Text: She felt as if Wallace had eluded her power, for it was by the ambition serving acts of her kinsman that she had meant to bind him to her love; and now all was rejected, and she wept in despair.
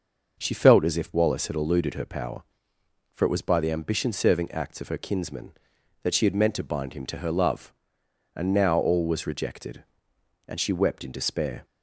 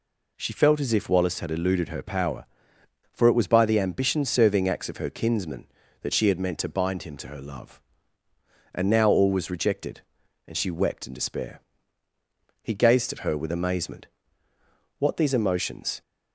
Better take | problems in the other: first | goes on to say "He gazed at her with amazement What these emotions"; strong; from 12.6 s on; 3.4 s long

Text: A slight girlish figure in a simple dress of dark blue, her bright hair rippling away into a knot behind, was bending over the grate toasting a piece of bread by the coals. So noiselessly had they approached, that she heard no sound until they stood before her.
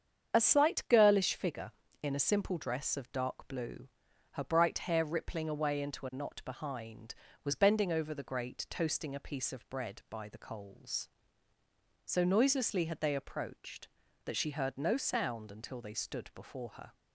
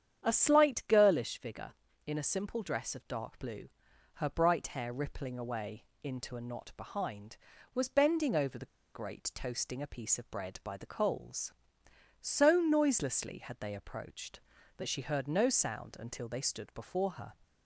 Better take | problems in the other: first | starts louder than the rest; strong; until 1.3 s; 9 dB; strong in the first // pauses between "away" and "into"; slight; at 5.8 s; 0.18 s long // pauses between "the" and "grate"; slight; at 8.6 s; 0.28 s long

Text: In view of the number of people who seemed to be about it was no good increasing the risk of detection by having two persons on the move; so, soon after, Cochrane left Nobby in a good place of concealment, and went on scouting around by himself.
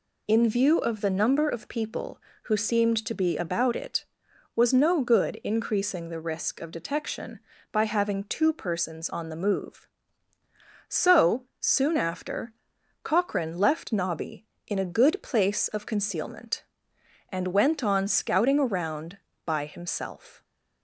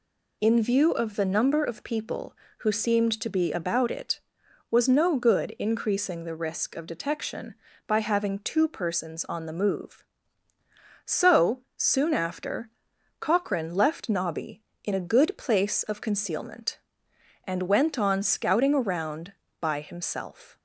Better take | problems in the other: neither | none

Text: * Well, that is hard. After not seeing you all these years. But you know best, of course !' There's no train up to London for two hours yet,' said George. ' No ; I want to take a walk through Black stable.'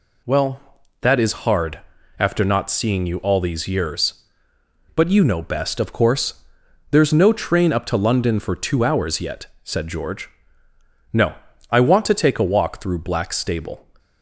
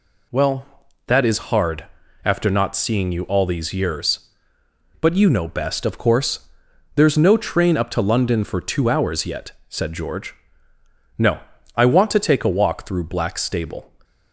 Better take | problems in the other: neither | none

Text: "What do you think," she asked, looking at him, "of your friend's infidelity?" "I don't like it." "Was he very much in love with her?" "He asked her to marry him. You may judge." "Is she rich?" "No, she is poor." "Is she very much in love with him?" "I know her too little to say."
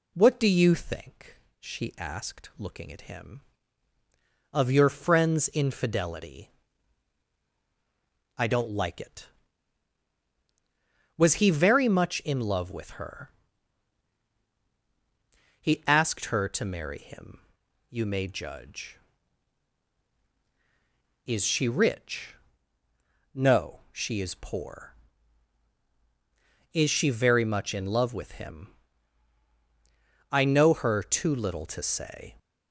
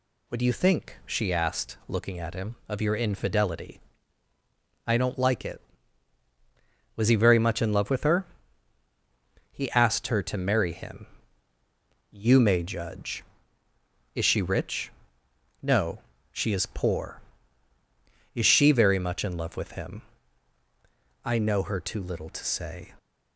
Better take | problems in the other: first | skips "friend's"; at 2.9 s

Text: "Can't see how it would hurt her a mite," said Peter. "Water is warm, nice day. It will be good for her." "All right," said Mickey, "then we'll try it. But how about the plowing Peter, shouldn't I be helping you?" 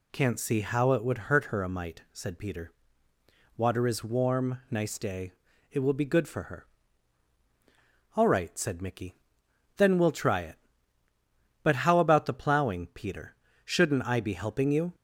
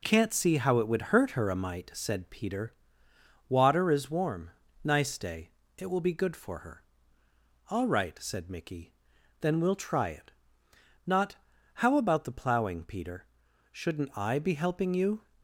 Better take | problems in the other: first | says "Not" for "But"; at 11.0 s

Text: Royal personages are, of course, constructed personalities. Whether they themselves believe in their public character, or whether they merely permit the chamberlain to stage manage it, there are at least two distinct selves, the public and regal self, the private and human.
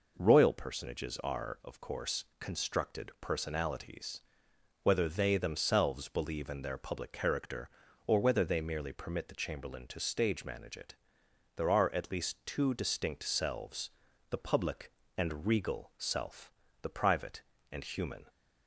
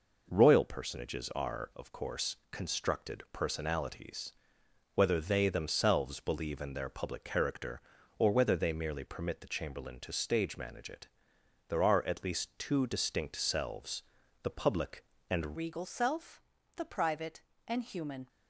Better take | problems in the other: first | changes voice at "regal"; from 15.5 s on; 2.7 s long

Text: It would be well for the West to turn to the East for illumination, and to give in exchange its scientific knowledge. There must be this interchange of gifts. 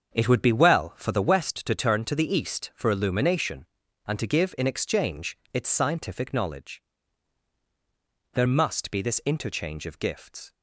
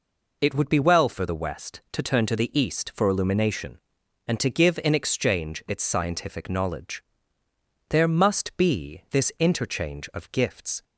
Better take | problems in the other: second | starts louder than the rest; until 1.4 s; 7 dB // pauses between "exchange" and "its"; slight; at 5.3 s; 0.16 s long

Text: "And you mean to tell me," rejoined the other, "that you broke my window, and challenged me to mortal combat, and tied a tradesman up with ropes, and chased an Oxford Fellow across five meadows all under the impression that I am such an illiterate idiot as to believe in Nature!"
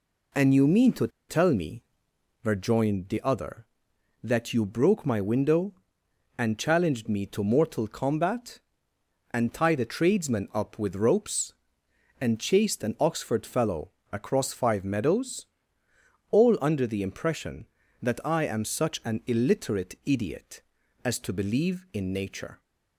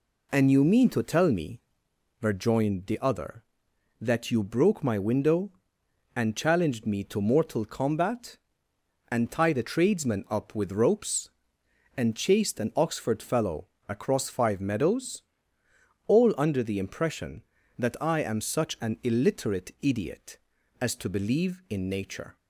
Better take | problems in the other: second | pauses between "to" and "tell"; slight; at 1.0 s; 0.20 s long // pauses between "Fellow" and "across"; slight; at 13.8 s; 0.22 s long; slight in the second // pauses between "meadows" and "all"; noticeable; at 15.4 s; 0.84 s long; noticeable in the second

